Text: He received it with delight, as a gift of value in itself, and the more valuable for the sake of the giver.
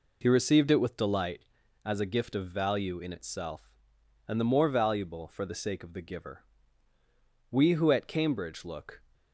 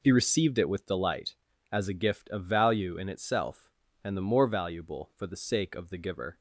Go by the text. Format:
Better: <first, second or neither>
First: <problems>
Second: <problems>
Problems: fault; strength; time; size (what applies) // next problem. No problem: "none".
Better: second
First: goes on to say "We who at Cambridge look"; from 7.4 s on; 1.5 s long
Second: none